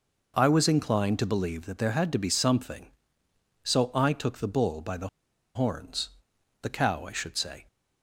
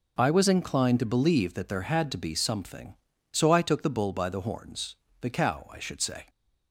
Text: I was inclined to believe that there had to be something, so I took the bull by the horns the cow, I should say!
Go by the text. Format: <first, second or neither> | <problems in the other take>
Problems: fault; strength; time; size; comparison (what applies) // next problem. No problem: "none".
second | pauses between "the" and "horns"; noticeable; at 5.0 s; 0.48 s long // pauses between "horns" and "the"; noticeable; at 6.0 s; 0.54 s long; slight in the second